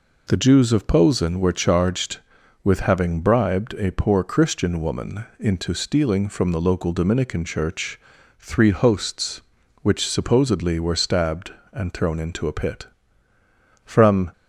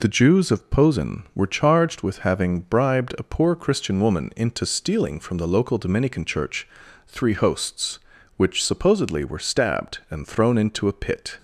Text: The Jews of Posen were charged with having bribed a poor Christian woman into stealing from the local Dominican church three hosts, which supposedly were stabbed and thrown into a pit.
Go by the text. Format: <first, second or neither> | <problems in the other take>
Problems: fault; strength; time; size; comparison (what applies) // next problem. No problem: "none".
second | pauses between "woman" and "into"; slight; at 5.2 s; 0.16 s long // pauses between "church" and "three"; at 7.9 s; 0.40 s long; also in the second // goes on to say "From"; slight; from 13.8 s on; 0.46 s long